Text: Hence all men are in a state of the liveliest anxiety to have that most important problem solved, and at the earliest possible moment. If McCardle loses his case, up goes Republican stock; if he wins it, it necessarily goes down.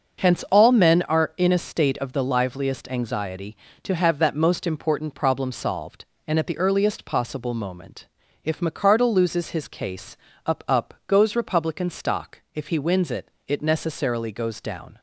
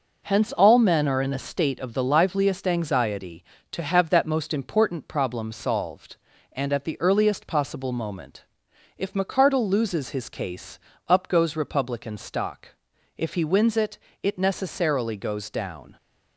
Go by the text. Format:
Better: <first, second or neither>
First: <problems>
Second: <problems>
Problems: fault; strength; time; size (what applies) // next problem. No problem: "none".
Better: second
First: starts louder than the rest; noticeable; until 1.3 s; 6 dB // says "up" twice; at 10.6 s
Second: none